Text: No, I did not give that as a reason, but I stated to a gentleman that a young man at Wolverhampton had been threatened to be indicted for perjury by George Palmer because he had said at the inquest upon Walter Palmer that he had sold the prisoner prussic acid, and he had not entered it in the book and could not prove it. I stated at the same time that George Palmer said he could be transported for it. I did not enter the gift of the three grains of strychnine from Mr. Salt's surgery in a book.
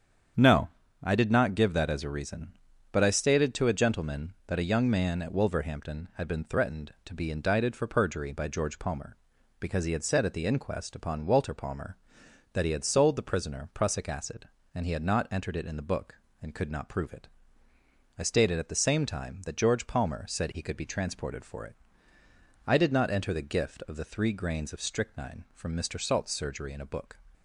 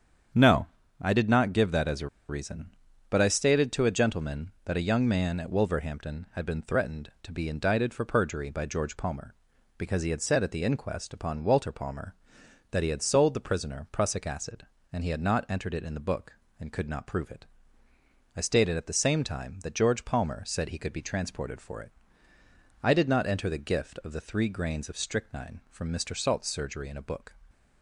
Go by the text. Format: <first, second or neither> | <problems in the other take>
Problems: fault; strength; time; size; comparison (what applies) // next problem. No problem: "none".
first | starts louder than the rest; strong; until 1.6 s; 8 dB; strong in the first // pauses between "a" and "reason"; slight; at 2.0 s; 0.22 s long